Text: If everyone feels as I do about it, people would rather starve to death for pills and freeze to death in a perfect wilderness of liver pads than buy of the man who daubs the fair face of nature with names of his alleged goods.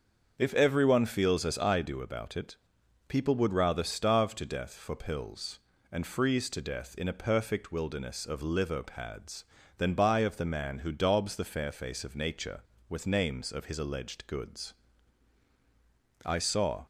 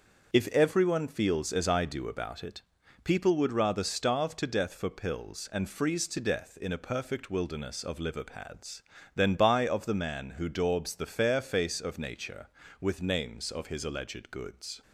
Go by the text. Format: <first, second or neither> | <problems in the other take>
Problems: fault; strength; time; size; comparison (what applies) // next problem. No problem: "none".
second | starts louder than the rest; until 1.3 s; 6.5 dB; also in the second // goes on to say "I saw"; from 16.2 s on; 0.60 s long